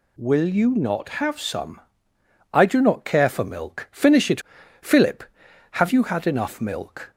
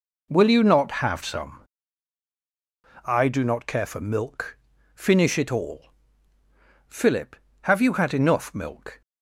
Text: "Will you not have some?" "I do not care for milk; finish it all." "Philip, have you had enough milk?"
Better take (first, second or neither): second